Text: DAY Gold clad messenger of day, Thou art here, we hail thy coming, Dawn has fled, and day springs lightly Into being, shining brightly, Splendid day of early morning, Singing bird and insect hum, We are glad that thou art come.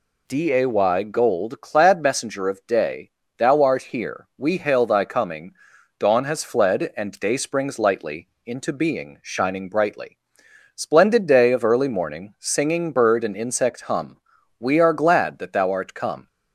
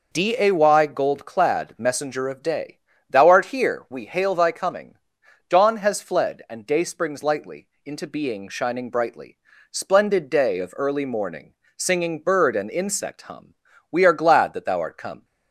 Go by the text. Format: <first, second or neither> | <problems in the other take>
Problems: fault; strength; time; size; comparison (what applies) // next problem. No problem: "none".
neither | pauses between "lightly" and "Into"; slight; the same in both